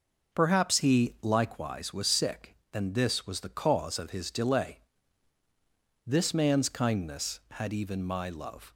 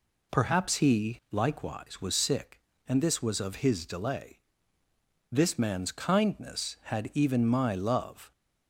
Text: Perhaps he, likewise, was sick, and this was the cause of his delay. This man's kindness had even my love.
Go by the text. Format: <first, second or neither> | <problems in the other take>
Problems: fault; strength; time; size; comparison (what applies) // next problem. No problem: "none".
first | skips "the cause"; at 3.3 s